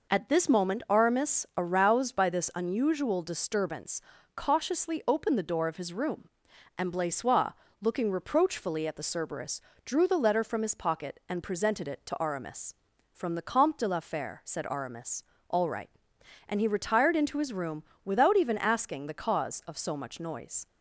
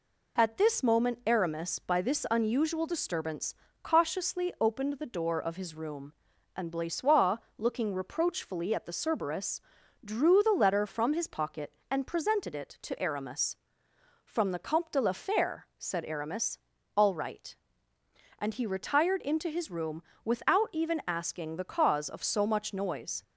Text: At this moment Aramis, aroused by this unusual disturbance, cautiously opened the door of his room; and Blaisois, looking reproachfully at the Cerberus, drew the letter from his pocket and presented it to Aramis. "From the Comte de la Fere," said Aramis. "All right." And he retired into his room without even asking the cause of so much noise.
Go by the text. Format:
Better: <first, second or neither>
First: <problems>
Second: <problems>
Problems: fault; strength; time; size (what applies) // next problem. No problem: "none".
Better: first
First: pauses between "room" and "without"; slight; at 17.8 s; 0.20 s long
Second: skips "aroused"; at 1.7 s // pauses between "room" and "without"; slight; at 20.0 s; 0.20 s long